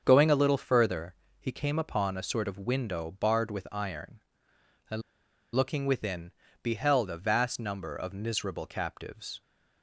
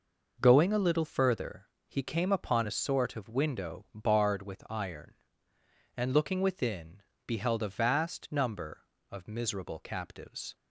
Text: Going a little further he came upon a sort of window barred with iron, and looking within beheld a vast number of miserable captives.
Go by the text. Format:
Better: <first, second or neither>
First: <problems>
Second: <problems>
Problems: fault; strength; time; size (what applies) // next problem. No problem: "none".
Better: second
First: starts louder than the rest; until 1.0 s; 7 dB // pauses between "further" and "he"; slight; at 1.1 s; 0.24 s long // pauses between "and" and "looking"; noticeable; at 5.0 s; 0.53 s long // pauses between "within" and "beheld"; slight; at 6.2 s; 0.32 s long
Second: pauses between "further" and "he"; slight; at 1.6 s; 0.18 s long // pauses between "within" and "beheld"; slight; at 7.0 s; 0.24 s long